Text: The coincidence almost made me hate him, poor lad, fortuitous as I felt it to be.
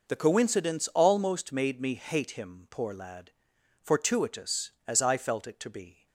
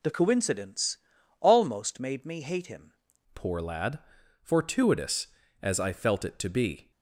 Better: first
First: none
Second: pauses between "coincidence" and "almost"; at 0.9 s; 0.42 s long // changes voice at "poor"; from 3.3 s on; 3.6 s long

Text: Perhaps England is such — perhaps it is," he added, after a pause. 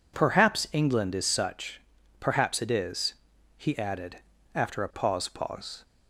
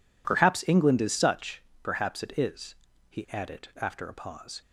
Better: second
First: says "pause" twice; at 5.2 s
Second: none

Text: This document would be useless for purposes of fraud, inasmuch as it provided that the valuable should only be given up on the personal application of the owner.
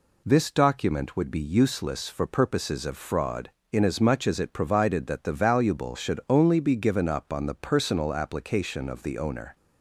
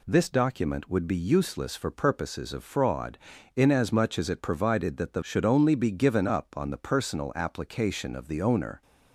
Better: first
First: none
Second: skips "valuable"; at 5.2 s

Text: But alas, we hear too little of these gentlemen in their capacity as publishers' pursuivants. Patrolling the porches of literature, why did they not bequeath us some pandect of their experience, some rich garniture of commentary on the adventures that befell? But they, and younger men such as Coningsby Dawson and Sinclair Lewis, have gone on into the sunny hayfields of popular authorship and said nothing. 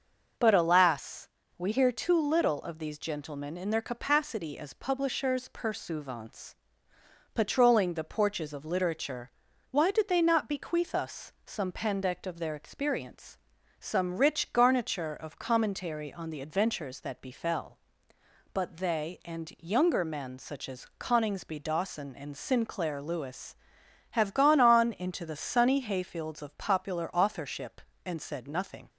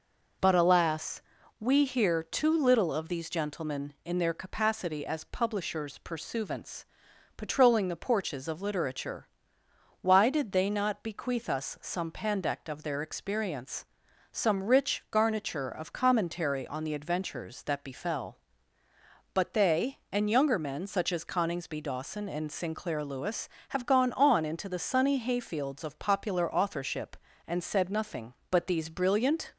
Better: first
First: none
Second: goes on to say "But these brilliant"; noticeable; from 28.4 s on; 1.0 s long

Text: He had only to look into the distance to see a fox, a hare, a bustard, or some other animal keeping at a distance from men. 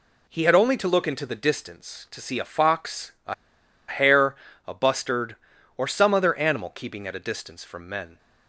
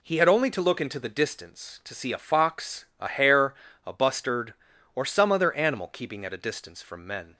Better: second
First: pauses between "a" and "hare"; noticeable; at 3.3 s; 0.54 s long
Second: none

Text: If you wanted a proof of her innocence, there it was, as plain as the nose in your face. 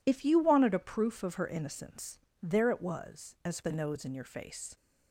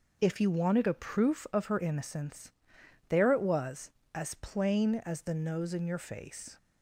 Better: second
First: skips "plain as"; at 3.6 s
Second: none

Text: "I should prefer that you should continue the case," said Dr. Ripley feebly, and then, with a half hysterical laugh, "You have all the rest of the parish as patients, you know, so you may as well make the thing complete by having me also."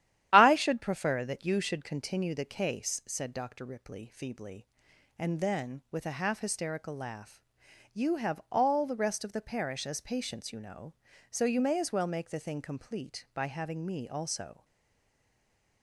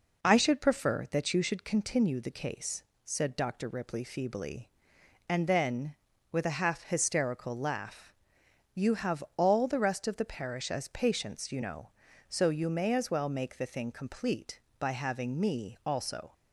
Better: second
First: starts louder than the rest; strong; until 1.3 s; 11.5 dB // stays silent after the last word; noticeable; from 14.6 s on; 1.2 s long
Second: none

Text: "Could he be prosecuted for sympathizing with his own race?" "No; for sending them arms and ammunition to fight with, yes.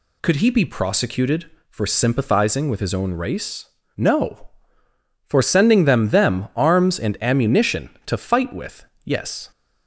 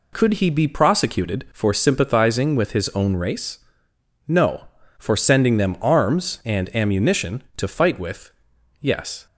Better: second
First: says "them" twice; at 6.0 s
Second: none

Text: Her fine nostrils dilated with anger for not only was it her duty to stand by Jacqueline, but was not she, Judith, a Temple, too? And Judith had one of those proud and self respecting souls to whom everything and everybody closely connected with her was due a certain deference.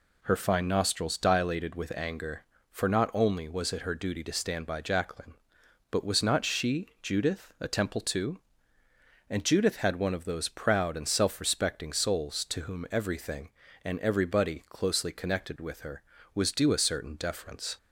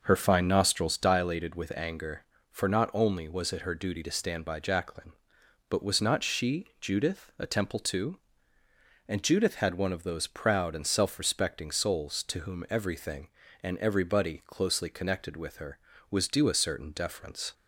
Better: first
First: none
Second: starts louder than the rest; noticeable; until 1.1 s; 5.5 dB

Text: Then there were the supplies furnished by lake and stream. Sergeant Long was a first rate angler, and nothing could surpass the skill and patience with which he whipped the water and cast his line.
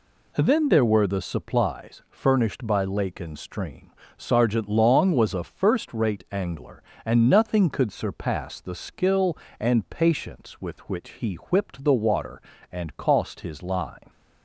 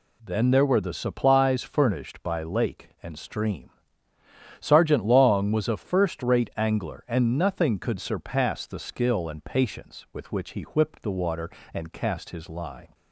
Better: second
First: says "cost" for "cast"; at 12.9 s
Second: none

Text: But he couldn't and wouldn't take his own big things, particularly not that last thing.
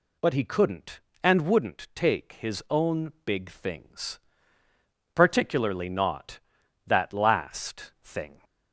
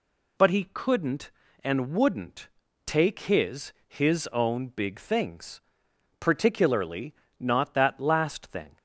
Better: first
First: none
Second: pauses between "wouldn't" and "take"; at 2.4 s; 0.38 s long // says "his" twice; at 3.8 s // pauses between "particularly" and "not"; slight; at 7.1 s; 0.24 s long

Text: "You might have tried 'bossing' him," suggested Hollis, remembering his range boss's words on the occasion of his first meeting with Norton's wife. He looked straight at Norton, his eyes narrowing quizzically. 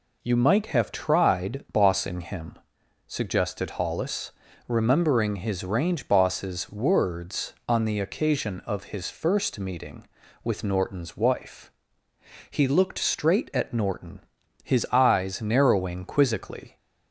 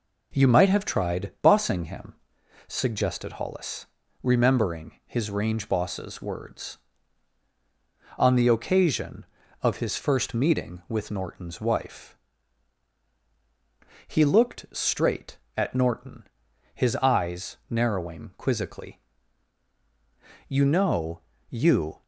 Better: first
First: none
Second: goes on to say "You know you"; from 20.4 s on; 1.5 s long

